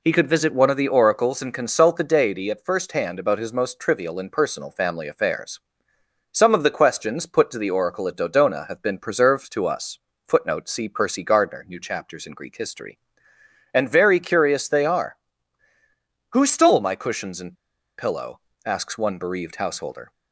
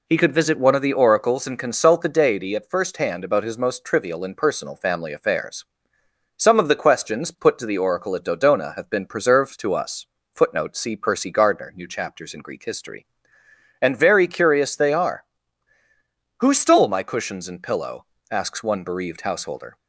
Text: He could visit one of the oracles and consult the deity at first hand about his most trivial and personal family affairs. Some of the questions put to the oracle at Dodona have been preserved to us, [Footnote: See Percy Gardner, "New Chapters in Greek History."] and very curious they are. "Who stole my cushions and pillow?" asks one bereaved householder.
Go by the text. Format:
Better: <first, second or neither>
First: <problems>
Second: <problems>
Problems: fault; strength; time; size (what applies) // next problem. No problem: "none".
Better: second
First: pauses between "and" and "pillow"; at 17.5 s; 0.42 s long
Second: none